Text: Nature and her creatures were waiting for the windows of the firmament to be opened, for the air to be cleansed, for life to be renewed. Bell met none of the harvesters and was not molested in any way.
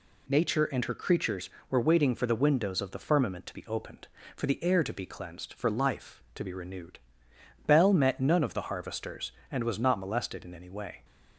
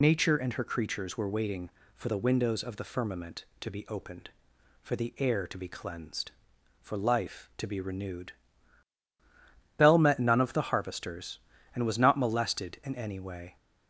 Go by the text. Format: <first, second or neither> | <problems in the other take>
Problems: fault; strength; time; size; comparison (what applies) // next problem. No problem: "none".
first | loses the start of "Nature"; at 0.0 s; 50 ms